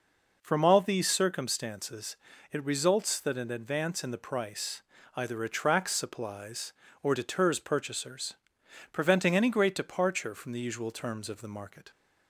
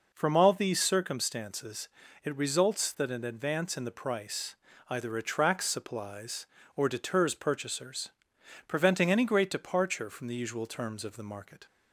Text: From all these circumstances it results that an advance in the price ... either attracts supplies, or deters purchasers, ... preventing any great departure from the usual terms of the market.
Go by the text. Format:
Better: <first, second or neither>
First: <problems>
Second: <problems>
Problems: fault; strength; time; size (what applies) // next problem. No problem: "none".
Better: neither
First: pauses between "circumstances" and "it"; slight; at 2.1 s; 0.34 s long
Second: pauses between "circumstances" and "it"; slight; at 1.8 s; 0.34 s long